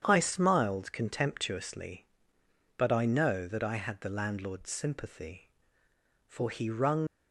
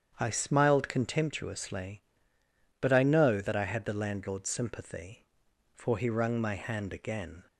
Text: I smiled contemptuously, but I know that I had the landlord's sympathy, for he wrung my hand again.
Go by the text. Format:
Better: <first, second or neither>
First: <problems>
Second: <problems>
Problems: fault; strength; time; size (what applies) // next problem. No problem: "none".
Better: second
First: starts louder than the rest; strong; until 1.0 s; 8.5 dB // stops before "my hand again"; at 7.0 s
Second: starts louder than the rest; strong; until 1.2 s; 8 dB